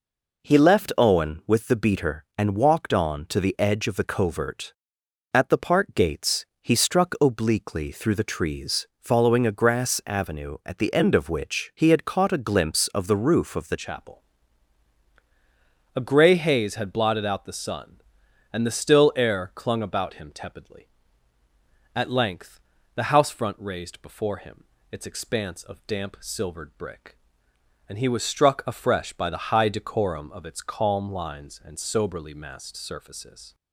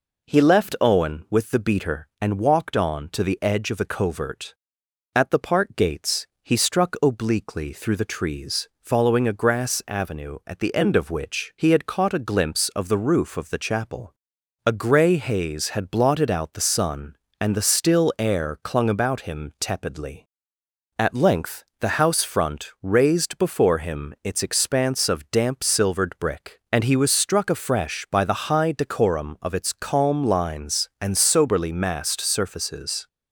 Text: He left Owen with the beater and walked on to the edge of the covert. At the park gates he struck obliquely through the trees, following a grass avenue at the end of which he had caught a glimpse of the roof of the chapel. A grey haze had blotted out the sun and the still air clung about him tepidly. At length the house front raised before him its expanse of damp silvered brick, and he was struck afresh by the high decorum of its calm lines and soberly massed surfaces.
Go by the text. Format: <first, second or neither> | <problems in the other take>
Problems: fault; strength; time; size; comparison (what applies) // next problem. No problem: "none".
second | pauses between "gates" and "he"; slight; at 6.4 s; 0.16 s long; slight in the second // changes voice at "chapel"; from 13.7 s on; 19.8 s long // pauses between "length" and "the"; slight; at 22.6 s; 0.36 s long; slight in the second // pauses between "him" and "its"; slight; at 24.6 s; 0.28 s long